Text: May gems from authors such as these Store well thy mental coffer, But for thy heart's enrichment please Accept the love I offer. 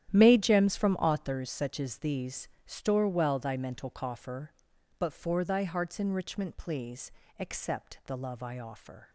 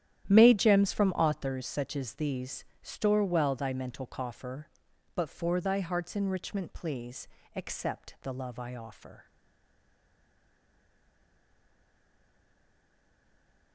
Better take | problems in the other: first | starts louder than the rest; strong; until 1.2 s; 11 dB; strong in the first // pauses between "these" and "Store"; slight; at 2.6 s; 0.18 s long; slight in the first // pauses between "please" and "Accept"; slight; at 7.2 s; 0.26 s long; slight in the first // stays silent after the last word; strong; from 9.2 s on; 4.5 s long

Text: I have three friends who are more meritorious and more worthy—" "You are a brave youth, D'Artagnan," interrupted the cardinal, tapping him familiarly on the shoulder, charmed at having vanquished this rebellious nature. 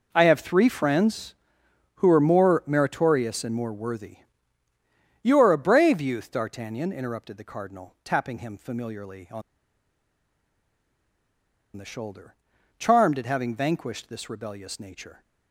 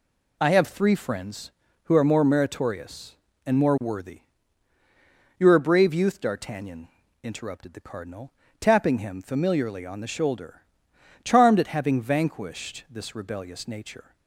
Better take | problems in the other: second | pauses between "on" and "the"; strong; at 9.4 s; 2.3 s long

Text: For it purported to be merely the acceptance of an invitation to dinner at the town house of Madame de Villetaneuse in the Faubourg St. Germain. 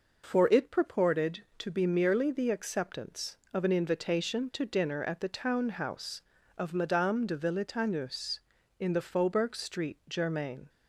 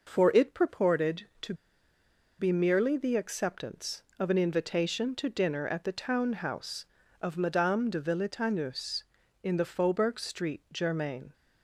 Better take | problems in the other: first | pauses between "to" and "be"; noticeable; at 1.5 s; 0.85 s long

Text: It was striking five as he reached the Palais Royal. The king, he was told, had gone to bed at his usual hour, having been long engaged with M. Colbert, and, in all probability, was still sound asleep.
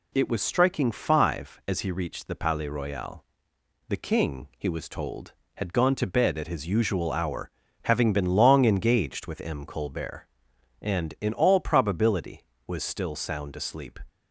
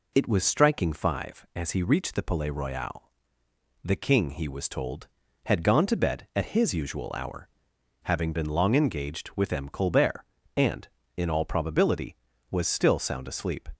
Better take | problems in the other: neither | none

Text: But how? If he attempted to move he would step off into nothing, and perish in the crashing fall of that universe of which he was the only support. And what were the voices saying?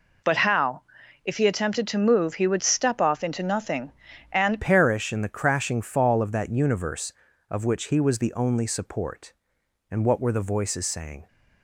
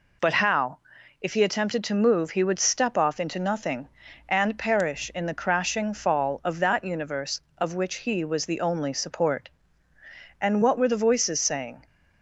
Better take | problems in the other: second | changes voice at "perish"; from 4.6 s on; 6.6 s long

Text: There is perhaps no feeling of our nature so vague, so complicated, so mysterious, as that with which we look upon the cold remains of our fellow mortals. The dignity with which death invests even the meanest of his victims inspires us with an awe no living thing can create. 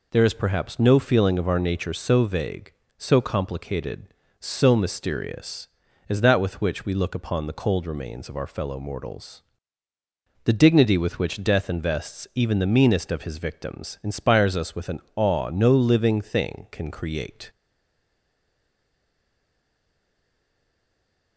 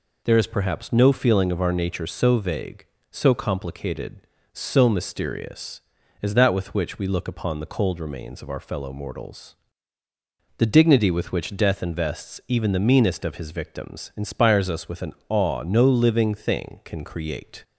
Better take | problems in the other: second | pauses between "an" and "awe"; slight; at 14.9 s; 0.16 s long; slight in the second // stays silent after the last word; strong; from 17.4 s on; 3.9 s long

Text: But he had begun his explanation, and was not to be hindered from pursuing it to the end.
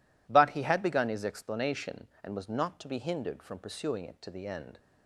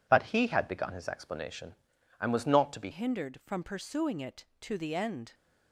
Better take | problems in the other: first | changes voice at "hindered"; from 2.9 s on; 2.4 s long

